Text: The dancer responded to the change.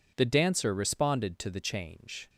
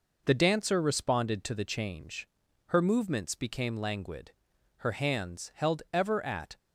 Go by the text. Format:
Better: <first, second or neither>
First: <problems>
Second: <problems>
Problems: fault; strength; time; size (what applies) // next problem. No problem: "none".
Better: first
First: none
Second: goes on to say "Her movements became languid Her hands held ever at"; strong; from 2.6 s on; 3.8 s long